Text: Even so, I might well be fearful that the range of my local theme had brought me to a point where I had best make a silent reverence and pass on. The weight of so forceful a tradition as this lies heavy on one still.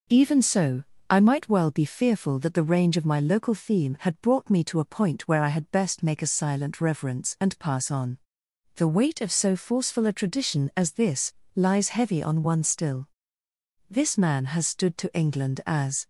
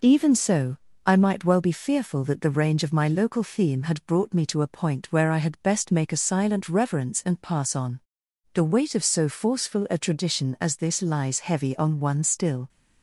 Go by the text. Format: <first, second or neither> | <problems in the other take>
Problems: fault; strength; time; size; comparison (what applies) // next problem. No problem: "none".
second | pauses between "this" and "lies"; slight; at 11.3 s; 0.22 s long // goes on to say "This man has stood to England as"; strong; from 13.8 s on; 2.1 s long